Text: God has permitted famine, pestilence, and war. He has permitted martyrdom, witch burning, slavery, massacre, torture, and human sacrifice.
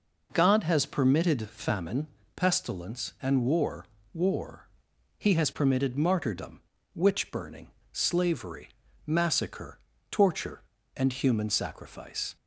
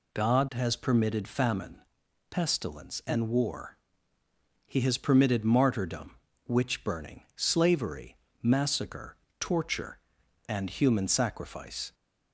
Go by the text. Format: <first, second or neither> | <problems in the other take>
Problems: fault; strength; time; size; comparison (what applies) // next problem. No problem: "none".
second | says "war" twice; at 4.1 s